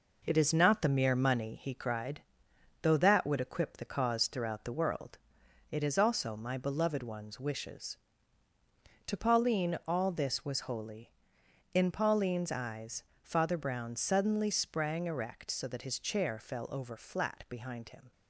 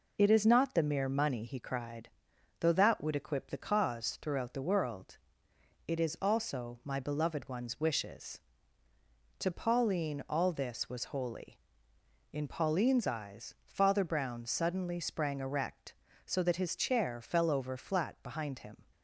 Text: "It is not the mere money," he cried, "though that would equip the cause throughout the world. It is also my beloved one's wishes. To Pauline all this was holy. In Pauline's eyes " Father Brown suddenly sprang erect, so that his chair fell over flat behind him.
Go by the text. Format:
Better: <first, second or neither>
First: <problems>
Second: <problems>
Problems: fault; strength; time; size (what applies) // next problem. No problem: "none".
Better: second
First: gets quieter; noticeable; throughout; 6 dB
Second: none